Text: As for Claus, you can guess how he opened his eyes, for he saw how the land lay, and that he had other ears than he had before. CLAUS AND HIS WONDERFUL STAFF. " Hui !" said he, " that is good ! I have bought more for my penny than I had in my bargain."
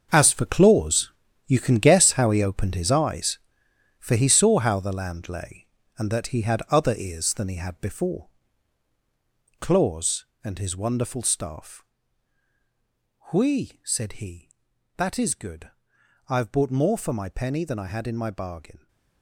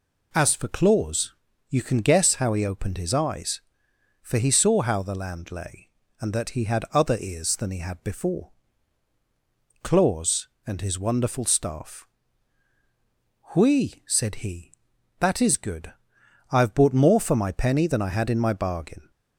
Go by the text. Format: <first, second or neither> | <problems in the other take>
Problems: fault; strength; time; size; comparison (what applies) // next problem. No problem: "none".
second | gets quieter; strong; throughout; 18 dB